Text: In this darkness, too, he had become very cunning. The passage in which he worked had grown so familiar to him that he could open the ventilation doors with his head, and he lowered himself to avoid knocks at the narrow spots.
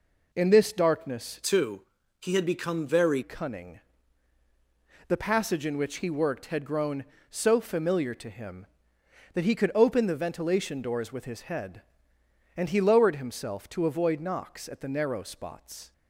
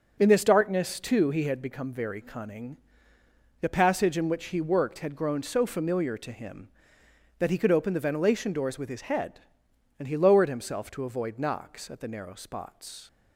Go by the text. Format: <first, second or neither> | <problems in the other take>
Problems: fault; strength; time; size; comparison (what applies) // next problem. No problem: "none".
second | changes voice from "too" to "very"; from 1.4 to 3.2 s; 1.8 s long